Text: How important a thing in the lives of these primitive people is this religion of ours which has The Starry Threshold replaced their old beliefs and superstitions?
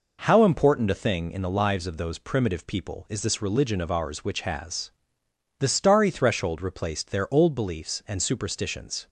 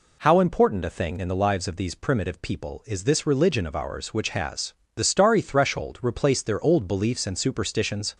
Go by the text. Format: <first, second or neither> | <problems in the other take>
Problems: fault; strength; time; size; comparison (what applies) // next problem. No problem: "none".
second | says "those" for "these"; at 1.9 s // pauses between "has" and "The"; noticeable; at 4.9 s; 0.68 s long; slight in the second